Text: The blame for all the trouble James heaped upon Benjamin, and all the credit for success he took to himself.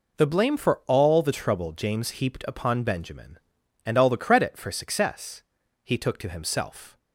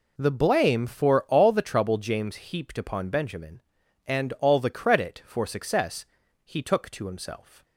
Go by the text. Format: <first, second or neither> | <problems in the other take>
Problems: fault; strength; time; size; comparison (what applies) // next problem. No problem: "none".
neither | pauses between "success" and "he"; the same in both